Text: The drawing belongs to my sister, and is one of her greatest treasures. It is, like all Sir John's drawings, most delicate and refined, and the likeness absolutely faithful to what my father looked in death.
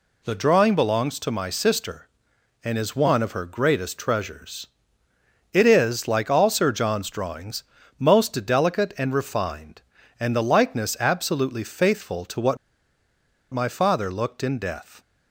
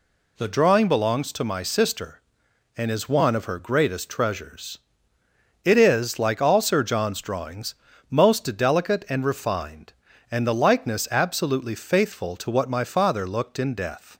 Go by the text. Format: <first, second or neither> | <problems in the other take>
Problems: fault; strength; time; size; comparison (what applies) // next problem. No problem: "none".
second | pauses between "what" and "my"; noticeable; at 12.5 s; 0.95 s long